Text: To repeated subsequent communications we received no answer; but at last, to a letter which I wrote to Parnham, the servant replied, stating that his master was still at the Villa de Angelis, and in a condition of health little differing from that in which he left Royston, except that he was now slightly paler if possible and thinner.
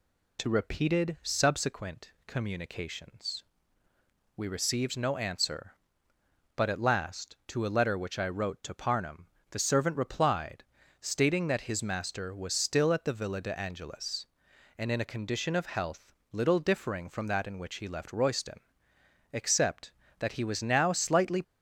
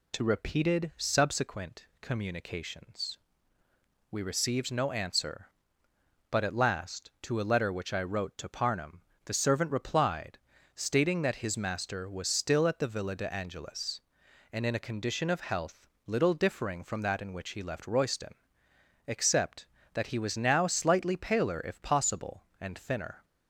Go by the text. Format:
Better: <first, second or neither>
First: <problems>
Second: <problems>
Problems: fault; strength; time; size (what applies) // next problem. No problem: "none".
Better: second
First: pauses between "communications" and "we"; noticeable; at 3.4 s; 0.94 s long // pauses between "health" and "little"; slight; at 16.1 s; 0.22 s long // stops before "paler if possible and thinner"; at 21.4 s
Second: pauses between "communications" and "we"; noticeable; at 3.1 s; 0.94 s long // pauses between "health" and "little"; slight; at 15.8 s; 0.22 s long